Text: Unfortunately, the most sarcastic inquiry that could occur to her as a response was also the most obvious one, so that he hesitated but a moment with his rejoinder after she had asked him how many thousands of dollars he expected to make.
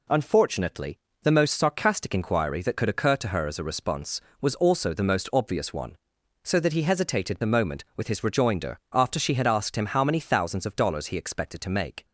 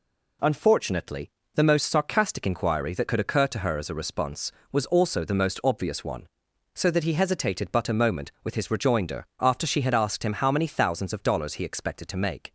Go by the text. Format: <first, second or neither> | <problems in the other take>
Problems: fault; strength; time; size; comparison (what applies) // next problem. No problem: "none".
second | skips "but"; at 7.4 s